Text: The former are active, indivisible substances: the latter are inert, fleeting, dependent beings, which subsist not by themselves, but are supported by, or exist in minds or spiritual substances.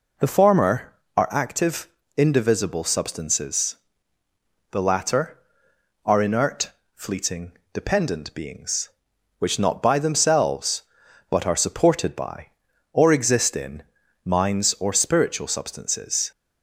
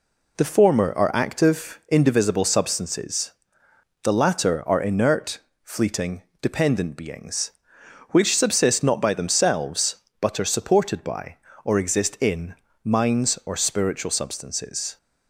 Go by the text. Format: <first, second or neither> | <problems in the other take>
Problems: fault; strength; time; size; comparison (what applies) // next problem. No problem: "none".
second | skips "subsist"; at 9.5 s // pauses between "in" and "minds"; at 13.8 s; 0.42 s long; slight in the second